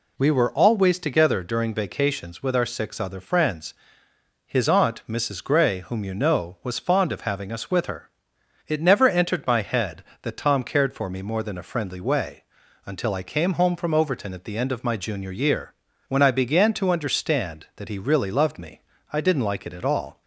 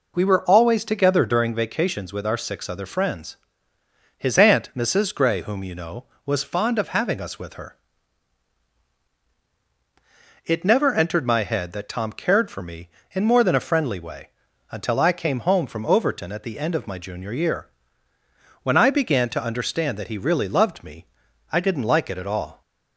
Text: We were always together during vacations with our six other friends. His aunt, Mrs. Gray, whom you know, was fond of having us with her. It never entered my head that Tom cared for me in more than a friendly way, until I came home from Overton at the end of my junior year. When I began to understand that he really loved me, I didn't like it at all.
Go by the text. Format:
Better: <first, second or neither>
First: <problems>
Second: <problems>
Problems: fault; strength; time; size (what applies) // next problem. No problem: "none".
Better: second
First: skips "in"; at 11.2 s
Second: none